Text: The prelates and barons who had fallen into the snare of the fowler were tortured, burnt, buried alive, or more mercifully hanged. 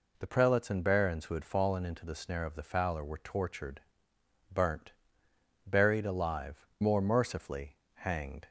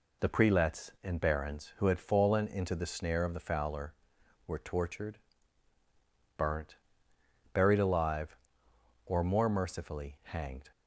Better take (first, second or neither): second